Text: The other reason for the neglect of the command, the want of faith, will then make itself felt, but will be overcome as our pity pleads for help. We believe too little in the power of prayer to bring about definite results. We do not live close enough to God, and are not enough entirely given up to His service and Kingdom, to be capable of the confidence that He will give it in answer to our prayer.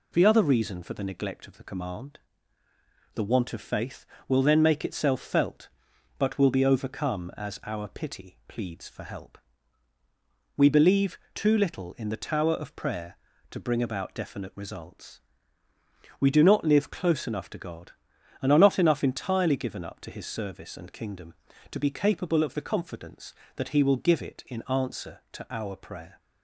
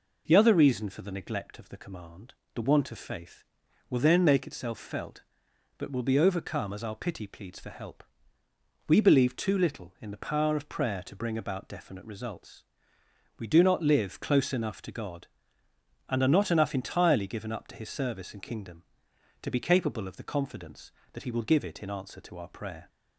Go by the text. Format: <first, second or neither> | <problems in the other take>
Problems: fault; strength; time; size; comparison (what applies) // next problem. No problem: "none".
second | pauses between "believe" and "too"; slight; at 11.1 s; 0.18 s long // says "tower" for "power"; at 12.1 s